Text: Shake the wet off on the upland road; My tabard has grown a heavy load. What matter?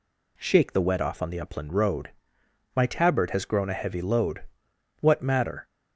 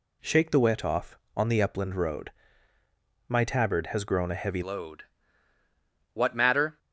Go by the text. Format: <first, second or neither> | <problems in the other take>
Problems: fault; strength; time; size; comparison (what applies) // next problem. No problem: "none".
first | changes voice at "load"; from 4.6 s on; 2.1 s long